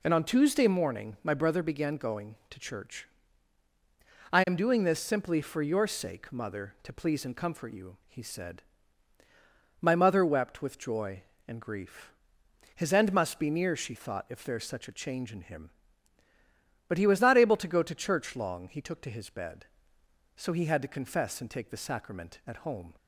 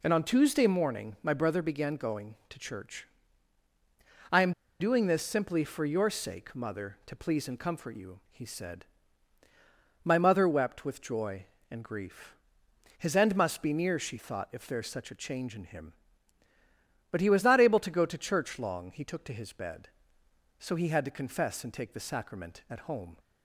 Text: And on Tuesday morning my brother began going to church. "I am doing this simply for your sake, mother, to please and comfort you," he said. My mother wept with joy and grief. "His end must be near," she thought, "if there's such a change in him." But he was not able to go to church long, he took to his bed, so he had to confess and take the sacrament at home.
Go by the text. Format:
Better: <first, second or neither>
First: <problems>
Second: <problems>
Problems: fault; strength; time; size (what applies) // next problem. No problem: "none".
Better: first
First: none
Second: pauses between "am" and "doing"; slight; at 4.5 s; 0.27 s long